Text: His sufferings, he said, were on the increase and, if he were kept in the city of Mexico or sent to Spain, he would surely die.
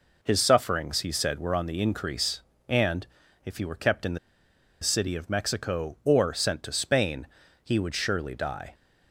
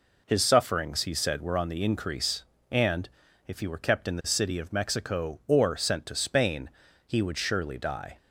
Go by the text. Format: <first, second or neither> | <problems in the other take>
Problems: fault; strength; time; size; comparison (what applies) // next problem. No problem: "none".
second | pauses between "the" and "city"; noticeable; at 4.1 s; 0.63 s long